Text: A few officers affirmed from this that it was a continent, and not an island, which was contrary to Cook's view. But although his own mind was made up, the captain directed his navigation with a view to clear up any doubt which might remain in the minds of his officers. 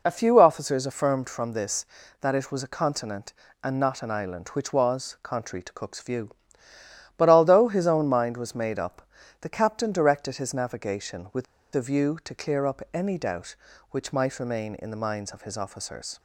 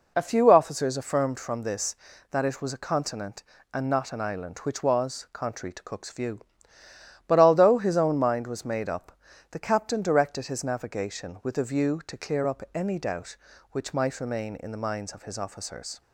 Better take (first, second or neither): second